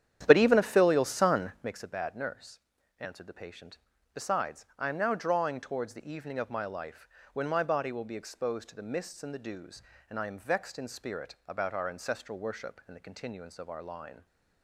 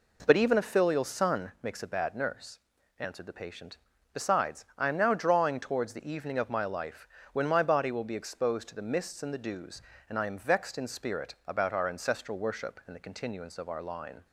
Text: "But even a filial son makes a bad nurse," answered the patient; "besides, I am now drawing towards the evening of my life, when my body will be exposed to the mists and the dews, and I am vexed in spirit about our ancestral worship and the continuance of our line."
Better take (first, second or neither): second